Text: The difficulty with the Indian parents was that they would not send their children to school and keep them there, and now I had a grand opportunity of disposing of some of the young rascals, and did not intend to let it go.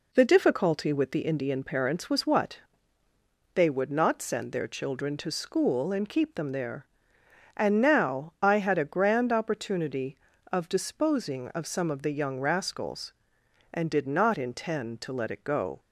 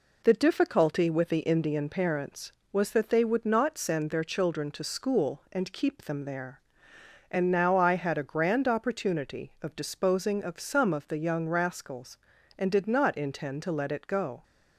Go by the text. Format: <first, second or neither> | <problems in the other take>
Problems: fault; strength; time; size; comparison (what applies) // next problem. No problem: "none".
second | says "what" for "that"; at 2.2 s